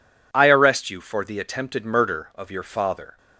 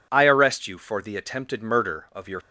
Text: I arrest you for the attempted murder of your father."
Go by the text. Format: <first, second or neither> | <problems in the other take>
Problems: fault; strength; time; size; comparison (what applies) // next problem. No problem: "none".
first | stops before "father"; at 2.4 s